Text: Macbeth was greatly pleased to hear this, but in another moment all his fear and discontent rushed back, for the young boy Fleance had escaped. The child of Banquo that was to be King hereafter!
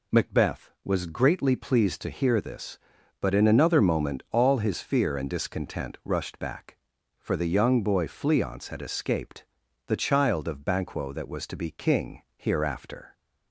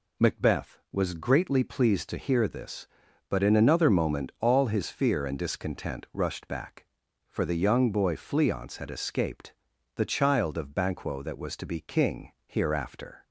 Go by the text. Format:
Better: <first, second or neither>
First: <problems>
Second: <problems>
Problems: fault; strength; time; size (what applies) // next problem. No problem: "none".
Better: neither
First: none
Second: none